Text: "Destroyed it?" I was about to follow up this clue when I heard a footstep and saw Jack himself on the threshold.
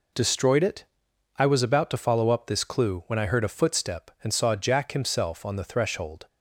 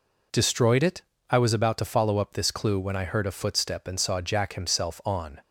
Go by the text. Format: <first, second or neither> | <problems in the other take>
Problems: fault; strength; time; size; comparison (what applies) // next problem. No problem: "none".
first | stops before "the threshold"; at 5.4 s